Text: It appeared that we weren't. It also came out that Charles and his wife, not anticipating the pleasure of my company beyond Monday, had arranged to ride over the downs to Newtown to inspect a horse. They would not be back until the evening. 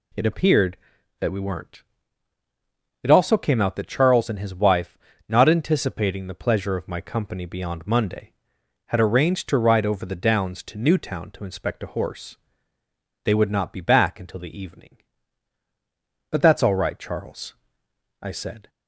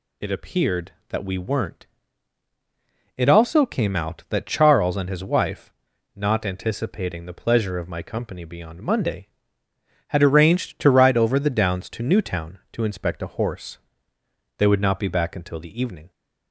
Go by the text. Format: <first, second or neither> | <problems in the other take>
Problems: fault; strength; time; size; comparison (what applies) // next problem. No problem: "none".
second | goes on to say "But that's all right Charles I said"; strong; from 16.2 s on; 2.4 s long